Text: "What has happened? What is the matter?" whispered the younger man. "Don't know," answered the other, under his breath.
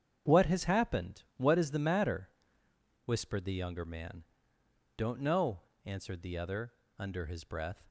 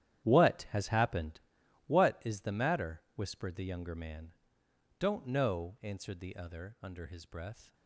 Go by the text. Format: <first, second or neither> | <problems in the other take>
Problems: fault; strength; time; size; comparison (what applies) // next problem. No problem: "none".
first | gets quieter; strong; throughout; 14 dB // starts louder than the rest; strong; until 1.2 s; 11 dB; strong in the first